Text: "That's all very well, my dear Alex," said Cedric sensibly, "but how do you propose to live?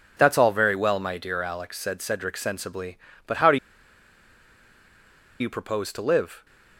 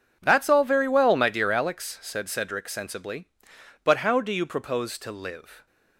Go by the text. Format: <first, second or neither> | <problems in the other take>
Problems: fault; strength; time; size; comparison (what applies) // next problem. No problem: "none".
second | pauses between "do" and "you"; strong; at 3.5 s; 1.8 s long